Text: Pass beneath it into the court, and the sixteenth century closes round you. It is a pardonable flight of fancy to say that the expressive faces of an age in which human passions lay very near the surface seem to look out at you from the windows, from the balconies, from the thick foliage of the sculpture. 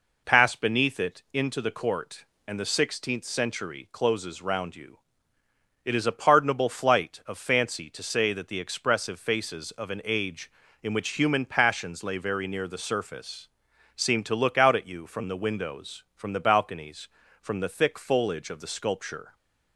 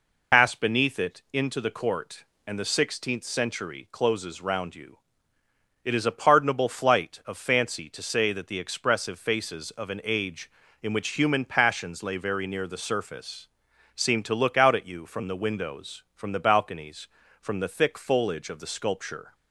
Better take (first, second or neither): first